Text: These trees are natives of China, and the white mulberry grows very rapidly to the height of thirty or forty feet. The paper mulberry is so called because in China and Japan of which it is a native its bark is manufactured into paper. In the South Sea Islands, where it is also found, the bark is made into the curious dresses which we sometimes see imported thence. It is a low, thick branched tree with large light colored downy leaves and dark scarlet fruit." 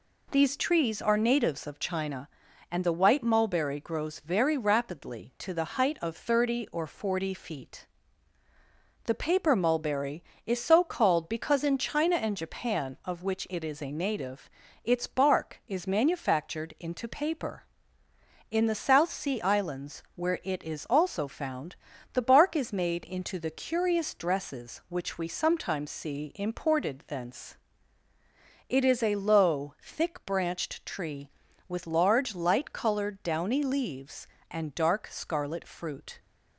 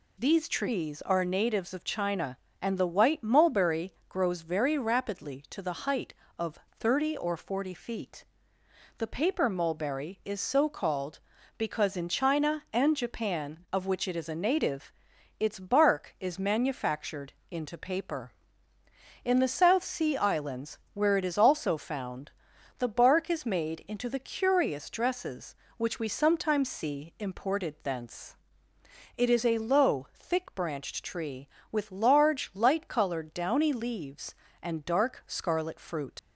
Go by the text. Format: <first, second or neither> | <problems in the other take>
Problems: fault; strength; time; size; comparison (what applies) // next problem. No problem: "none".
first | pauses between "mulberry" and "grows"; slight; at 3.9 s; 0.16 s long // pauses between "native" and "its"; noticeable; at 14.9 s; 0.48 s long; slight in the first // pauses between "manufactured" and "into"; slight; at 17.3 s; 0.18 s long // leaves "fruit" unfinished; at 36.1 s; 80 ms